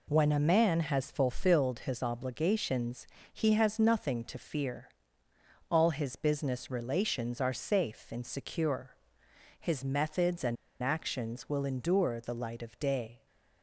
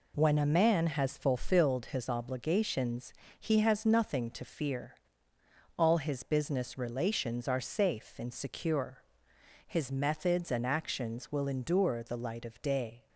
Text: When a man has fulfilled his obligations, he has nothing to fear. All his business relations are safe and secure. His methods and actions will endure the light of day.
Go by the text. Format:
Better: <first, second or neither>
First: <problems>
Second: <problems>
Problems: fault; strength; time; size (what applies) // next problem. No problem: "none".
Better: second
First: pauses between "and" and "actions"; slight; at 10.5 s; 0.25 s long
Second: none